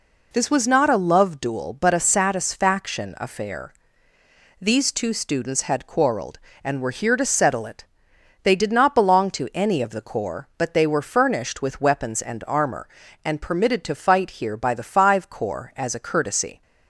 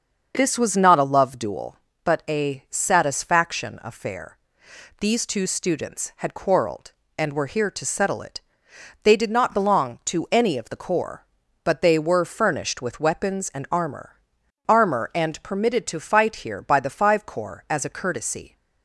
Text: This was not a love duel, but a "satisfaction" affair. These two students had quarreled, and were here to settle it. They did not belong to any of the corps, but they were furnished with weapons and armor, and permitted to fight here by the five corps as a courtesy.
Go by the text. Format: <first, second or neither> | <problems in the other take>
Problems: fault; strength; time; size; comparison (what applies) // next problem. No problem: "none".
first | starts louder than the rest; noticeable; until 1.3 s; 6 dB // says "armor" twice; at 14.6 s